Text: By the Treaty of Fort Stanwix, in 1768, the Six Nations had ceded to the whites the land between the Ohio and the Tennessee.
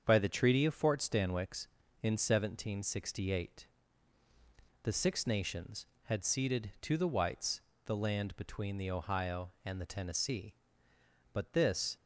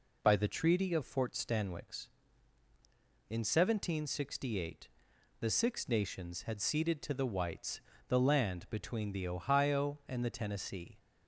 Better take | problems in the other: second | starts louder than the rest; strong; until 1.0 s; 7.5 dB // pauses between "whites" and "the"; slight; at 7.6 s; 0.24 s long; slight in the second // goes on to say "But this"; noticeable; from 11.3 s on; 0.64 s long

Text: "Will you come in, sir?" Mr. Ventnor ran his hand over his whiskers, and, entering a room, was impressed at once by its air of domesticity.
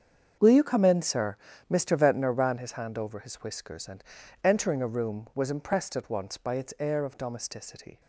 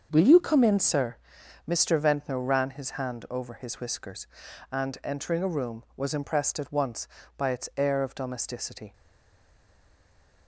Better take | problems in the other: first | starts louder than the rest; until 1.1 s; 6.5 dB; strong in the first // stays silent after the last word; noticeable; from 8.9 s on; 1.5 s long

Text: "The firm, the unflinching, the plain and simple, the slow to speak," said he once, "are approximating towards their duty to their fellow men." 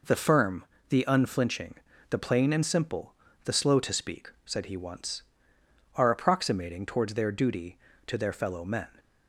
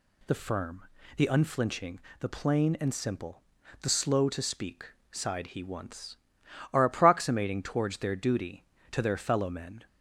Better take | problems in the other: first | says "sighed" for "said"; at 5.1 s

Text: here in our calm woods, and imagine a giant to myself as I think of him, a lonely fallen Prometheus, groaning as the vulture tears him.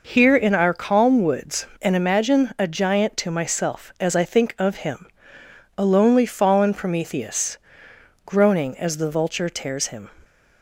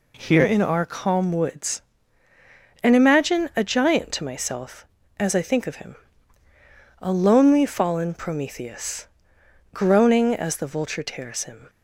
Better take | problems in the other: neither | none

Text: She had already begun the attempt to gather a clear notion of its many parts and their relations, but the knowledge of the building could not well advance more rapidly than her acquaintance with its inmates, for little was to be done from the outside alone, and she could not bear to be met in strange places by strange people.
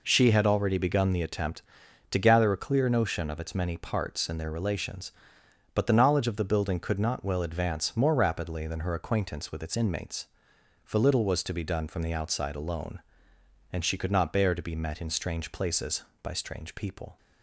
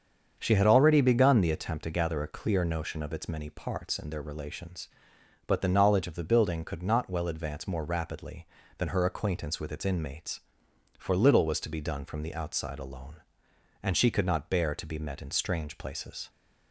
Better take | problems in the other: first | starts louder than the rest; strong; until 1.3 s; 7 dB // stops before "by strange people"; at 16.2 s

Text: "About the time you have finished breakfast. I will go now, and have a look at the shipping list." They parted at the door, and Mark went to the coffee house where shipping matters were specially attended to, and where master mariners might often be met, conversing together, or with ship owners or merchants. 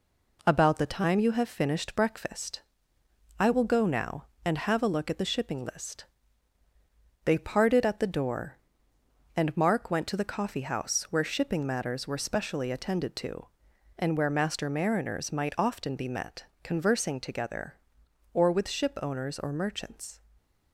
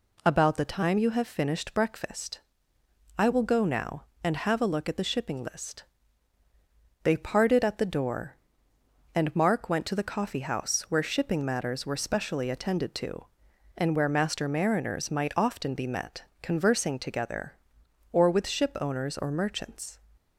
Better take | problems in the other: second | gets quieter; noticeable; throughout; 4 dB // stays silent after the last word; slight; from 20.1 s on; 0.6 s long

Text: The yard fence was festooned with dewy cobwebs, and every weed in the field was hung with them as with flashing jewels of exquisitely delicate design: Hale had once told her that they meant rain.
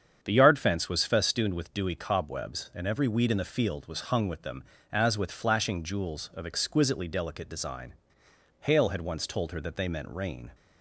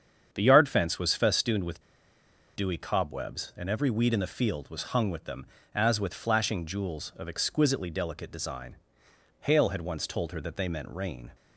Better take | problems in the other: first | starts louder than the rest; strong; until 1.3 s; 8 dB; strong in the first // pauses between "with" and "dewy"; noticeable; at 1.8 s; 0.73 s long

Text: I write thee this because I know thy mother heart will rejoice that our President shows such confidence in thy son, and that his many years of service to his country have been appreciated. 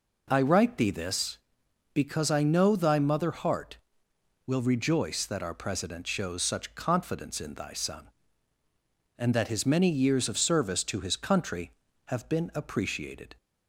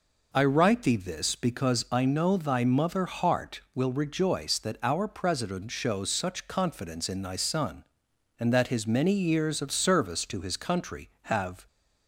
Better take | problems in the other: first | stops before "been appreciated"; at 11.6 s

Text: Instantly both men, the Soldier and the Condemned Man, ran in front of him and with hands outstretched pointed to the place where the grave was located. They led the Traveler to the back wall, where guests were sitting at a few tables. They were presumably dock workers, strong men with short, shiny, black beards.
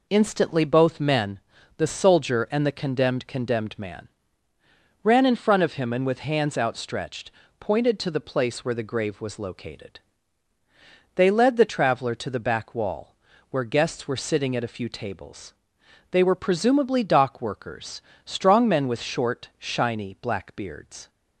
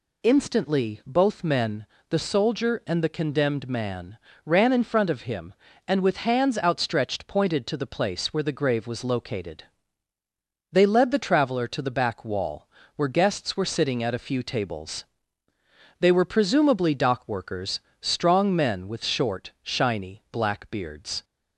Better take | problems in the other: second | says "Condemned" twice; at 3.2 s // pauses between "outstretched" and "pointed"; slight; at 7.2 s; 0.30 s long

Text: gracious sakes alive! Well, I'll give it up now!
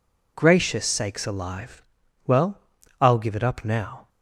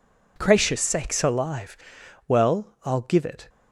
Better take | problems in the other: first | stops before "up now"; at 3.4 s

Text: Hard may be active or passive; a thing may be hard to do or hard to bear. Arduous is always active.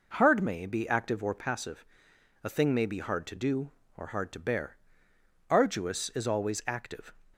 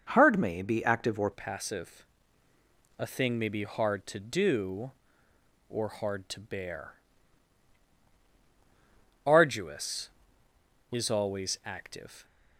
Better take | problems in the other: first | changes voice at "passive"; from 1.3 s on; 10.9 s long

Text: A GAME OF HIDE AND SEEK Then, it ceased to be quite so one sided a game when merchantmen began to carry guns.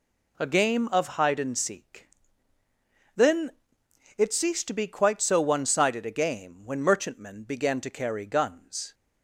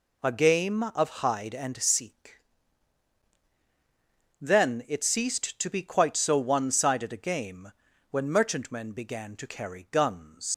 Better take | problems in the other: first | pauses between "SEEK" and "Then"; strong; at 2.4 s; 2.0 s long; also in the first // pauses between "game" and "when"; at 7.7 s; 0.40 s long // leaves "guns" unfinished; at 10.5 s; 125 ms

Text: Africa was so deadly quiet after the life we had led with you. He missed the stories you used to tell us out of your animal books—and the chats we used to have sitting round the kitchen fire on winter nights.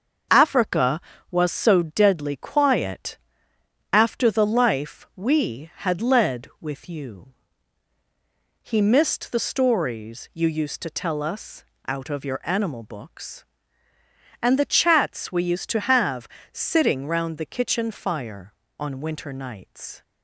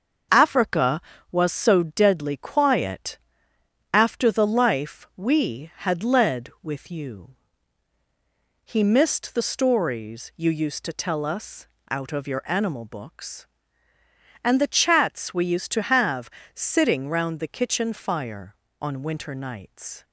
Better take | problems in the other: neither | starts louder than the rest; the same in both // pauses between "quiet" and "after"; noticeable; the same in both // pauses between "us" and "out"; slight; the same in both // pauses between "have" and "sitting"; slight; the same in both

